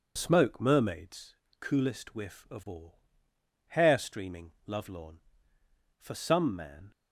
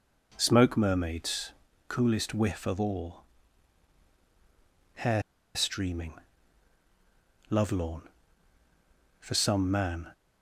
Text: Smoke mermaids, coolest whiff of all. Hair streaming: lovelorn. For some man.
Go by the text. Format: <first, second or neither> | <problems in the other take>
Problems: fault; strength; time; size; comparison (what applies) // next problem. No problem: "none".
first | pauses between "Hair" and "streaming"; slight; at 5.2 s; 0.33 s long